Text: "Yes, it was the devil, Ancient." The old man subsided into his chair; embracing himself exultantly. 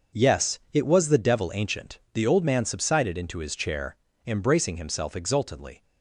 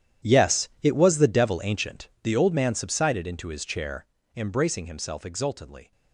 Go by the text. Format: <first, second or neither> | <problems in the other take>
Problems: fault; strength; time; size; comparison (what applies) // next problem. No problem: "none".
first | gets quieter; strong; throughout; 17 dB // starts louder than the rest; strong; until 1.3 s; 10.5 dB; noticeable in the first